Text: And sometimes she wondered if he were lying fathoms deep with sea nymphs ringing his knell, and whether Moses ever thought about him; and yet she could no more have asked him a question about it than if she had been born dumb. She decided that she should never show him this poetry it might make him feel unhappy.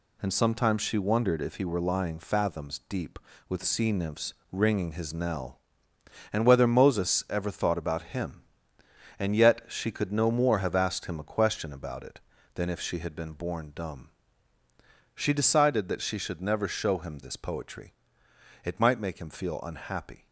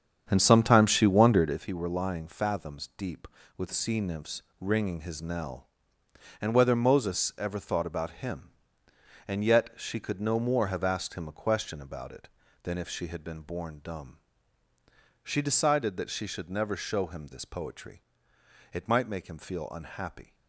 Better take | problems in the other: first | starts louder than the rest; strong; until 1.7 s; 8 dB // pauses between "nymphs" and "ringing"; slight; at 4.4 s; 0.16 s long; slight in the first // pauses between "poetry" and "it"; noticeable; at 18.0 s; 0.72 s long; noticeable in the first

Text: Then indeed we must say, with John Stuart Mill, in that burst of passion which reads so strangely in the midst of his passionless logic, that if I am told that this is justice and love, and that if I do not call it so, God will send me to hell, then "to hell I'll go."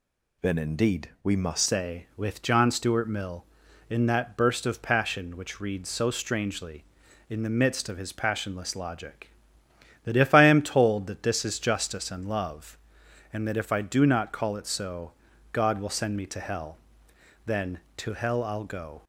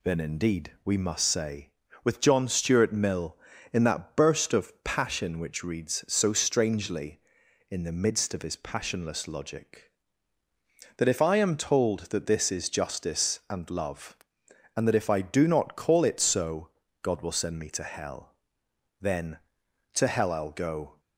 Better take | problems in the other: second | changes voice at "say"; from 1.6 s on; 17.4 s long

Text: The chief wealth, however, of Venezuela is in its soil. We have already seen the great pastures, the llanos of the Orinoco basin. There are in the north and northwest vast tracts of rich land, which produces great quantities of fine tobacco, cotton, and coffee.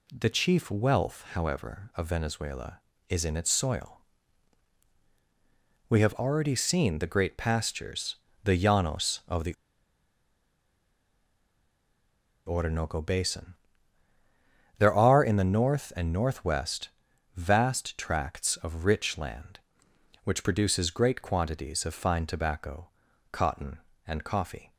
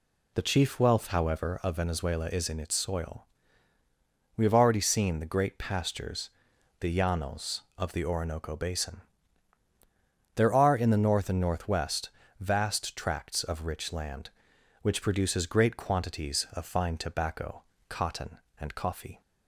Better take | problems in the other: second | pauses between "the" and "Orinoco"; strong; at 9.5 s; 2.9 s long // pauses between "northwest" and "vast"; noticeable; at 16.8 s; 0.46 s long; slight in the second

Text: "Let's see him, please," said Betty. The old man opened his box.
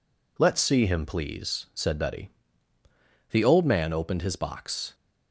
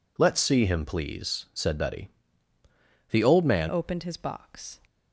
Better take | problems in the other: first | changes voice at "opened"; from 3.6 s on; 1.1 s long

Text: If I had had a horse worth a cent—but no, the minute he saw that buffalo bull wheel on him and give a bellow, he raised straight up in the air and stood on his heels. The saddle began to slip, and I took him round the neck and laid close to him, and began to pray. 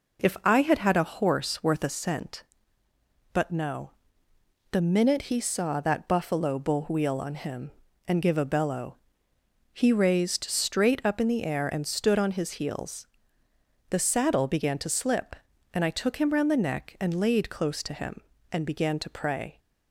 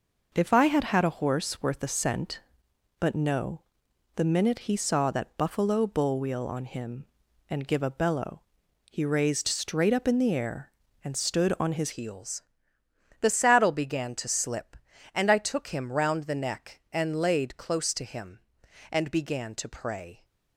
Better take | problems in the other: first | changes voice at "heels"; from 11.9 s on; 8.3 s long

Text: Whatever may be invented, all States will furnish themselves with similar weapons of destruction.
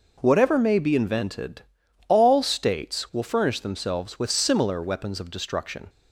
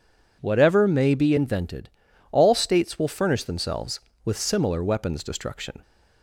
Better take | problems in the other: first | skips "of"; at 5.2 s

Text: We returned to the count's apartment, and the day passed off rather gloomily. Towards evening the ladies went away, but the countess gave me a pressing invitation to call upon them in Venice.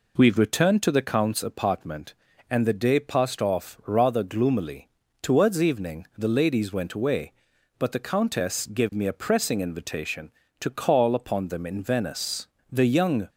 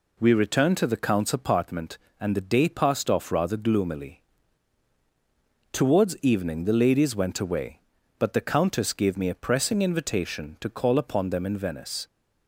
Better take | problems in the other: second | goes on to say "The young"; from 12.7 s on; 0.58 s long

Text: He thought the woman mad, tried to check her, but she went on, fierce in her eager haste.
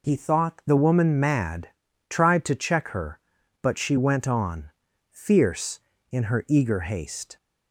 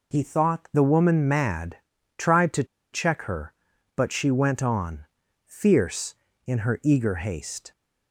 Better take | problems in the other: first | pauses between "to" and "check"; slight; at 2.6 s; 0.28 s long

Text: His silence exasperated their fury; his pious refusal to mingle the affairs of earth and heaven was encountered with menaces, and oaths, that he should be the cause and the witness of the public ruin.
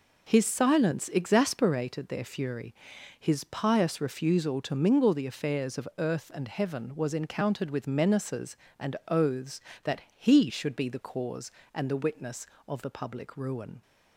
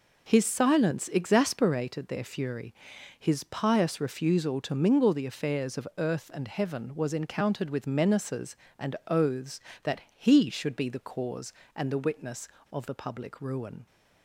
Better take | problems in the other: neither | pauses between "that" and "he"; slight; the same in both

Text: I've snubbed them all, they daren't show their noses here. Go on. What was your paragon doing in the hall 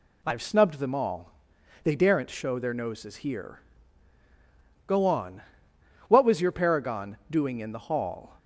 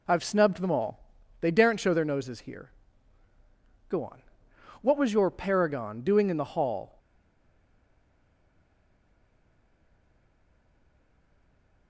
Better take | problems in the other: first | stays silent after the last word; strong; from 6.9 s on; 4.9 s long

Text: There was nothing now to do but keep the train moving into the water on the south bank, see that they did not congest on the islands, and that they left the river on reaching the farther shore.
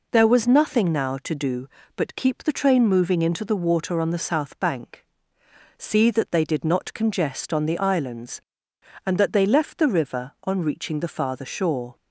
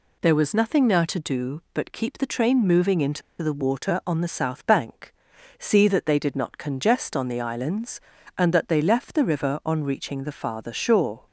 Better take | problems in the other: first | pauses between "into" and "the"; slight; at 3.2 s; 0.20 s long

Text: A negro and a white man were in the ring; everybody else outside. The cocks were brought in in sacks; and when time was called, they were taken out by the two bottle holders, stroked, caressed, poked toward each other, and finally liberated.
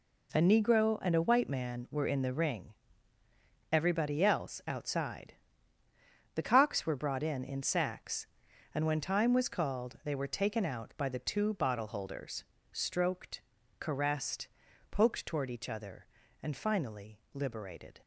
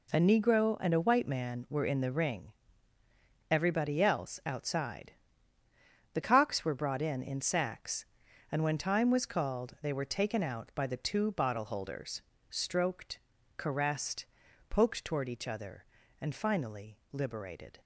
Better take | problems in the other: neither | none

